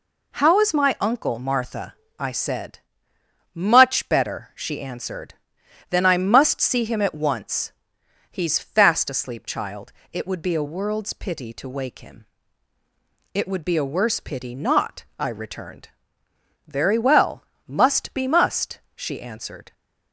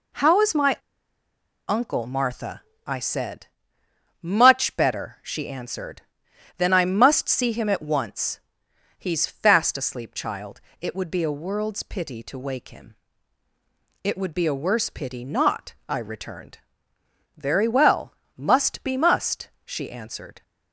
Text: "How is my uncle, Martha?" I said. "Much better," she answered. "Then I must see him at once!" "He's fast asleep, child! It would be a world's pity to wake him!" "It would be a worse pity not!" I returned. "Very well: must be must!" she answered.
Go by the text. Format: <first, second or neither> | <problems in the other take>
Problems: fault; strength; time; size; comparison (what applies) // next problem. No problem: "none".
first | pauses between "my" and "uncle"; noticeable; at 0.7 s; 0.90 s long